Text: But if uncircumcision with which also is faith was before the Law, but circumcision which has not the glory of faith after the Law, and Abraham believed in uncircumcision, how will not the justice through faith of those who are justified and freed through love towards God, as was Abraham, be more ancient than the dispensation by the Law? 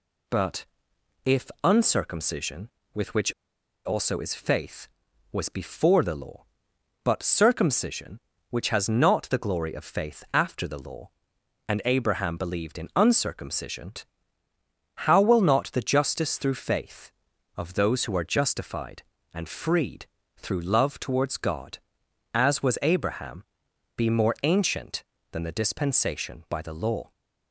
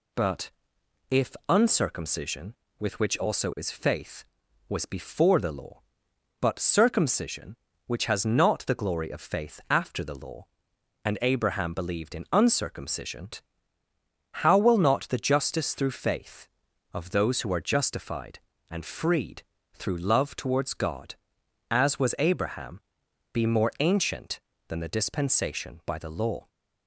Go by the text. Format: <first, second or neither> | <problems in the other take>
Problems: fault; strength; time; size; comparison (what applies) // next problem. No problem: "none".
second | pauses between "But" and "if"; noticeable; at 0.6 s; 0.60 s long; noticeable in the second // pauses between "if" and "uncircumcision"; slight; at 1.4 s; 0.16 s long; slight in the second // pauses between "which" and "also"; noticeable; at 3.3 s; 0.54 s long // pauses between "freed" and "through"; slight; at 20.0 s; 0.30 s long; slight in the second